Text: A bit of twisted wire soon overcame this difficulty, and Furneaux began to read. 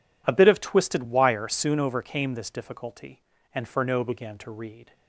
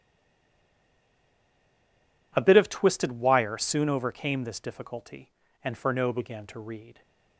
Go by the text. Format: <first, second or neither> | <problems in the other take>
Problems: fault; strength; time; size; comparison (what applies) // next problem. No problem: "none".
first | stays silent before the first word; until 2.3 s; 2.3 s long